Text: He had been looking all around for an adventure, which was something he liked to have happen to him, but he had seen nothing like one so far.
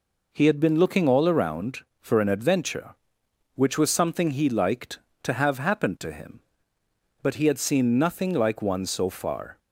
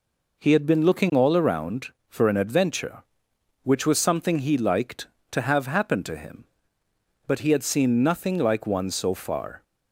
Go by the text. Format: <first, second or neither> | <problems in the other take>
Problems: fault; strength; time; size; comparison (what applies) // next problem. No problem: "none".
neither | none